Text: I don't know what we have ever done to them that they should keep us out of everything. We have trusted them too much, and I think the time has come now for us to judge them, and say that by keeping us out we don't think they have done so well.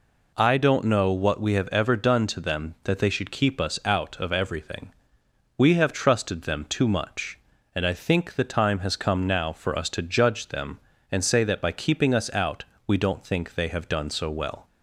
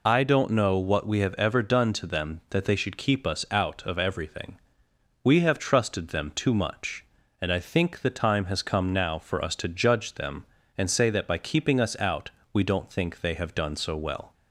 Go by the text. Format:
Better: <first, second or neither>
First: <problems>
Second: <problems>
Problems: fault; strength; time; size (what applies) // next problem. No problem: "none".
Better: first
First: pauses between "out" and "we"; slight; at 12.6 s; 0.22 s long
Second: loses the start of "I"; at 0.0 s; 45 ms // pauses between "out" and "we"; slight; at 12.3 s; 0.22 s long